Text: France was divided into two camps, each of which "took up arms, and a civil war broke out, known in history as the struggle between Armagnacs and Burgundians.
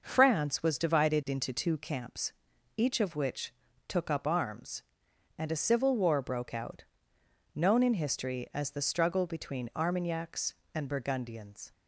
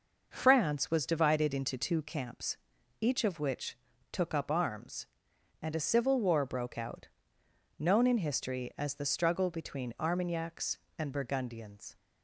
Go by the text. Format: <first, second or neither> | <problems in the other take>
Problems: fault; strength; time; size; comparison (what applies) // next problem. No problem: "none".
neither | pauses between "which" and "took"; the same in both